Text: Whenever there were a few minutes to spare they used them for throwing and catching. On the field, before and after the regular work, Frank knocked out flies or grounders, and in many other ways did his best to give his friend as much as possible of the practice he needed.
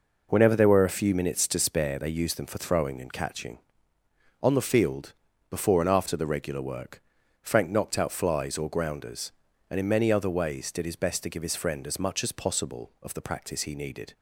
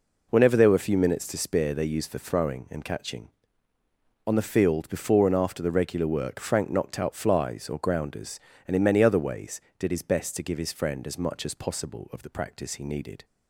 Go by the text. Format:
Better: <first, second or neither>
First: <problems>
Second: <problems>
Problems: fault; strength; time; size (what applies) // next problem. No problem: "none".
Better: first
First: none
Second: skips "them"; at 2.1 s